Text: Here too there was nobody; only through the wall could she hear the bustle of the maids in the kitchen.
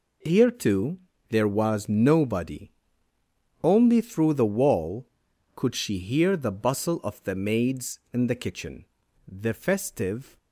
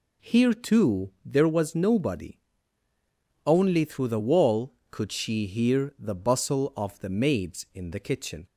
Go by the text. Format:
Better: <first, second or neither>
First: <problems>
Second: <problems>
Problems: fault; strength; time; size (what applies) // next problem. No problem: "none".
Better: second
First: pauses between "too" and "there"; slight; at 0.9 s; 0.32 s long // goes on to say "The festive"; noticeable; from 9.2 s on; 1.0 s long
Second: none